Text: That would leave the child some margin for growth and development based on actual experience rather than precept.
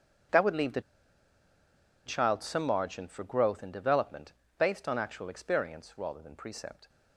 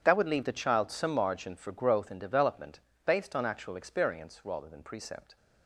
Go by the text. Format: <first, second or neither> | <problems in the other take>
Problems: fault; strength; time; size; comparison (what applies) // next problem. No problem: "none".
second | starts louder than the rest; strong; until 2.5 s; 8.5 dB; strong in the second // pauses between "the" and "child"; at 0.8 s; 1.2 s long // pauses between "development" and "based"; slight; at 4.3 s; 0.26 s long; slight in the second